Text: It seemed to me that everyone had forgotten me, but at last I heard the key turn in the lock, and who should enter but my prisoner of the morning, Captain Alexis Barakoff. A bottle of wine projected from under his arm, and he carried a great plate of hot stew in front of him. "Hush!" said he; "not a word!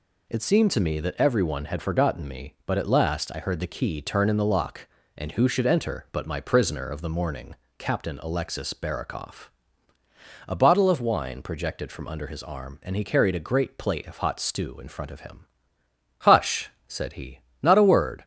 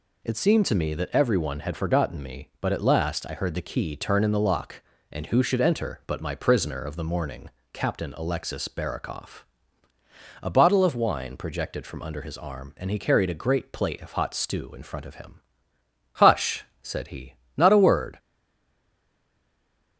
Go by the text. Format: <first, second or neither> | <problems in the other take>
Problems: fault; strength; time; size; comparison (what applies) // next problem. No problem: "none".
first | stays silent after the last word; noticeable; from 18.1 s on; 1.8 s long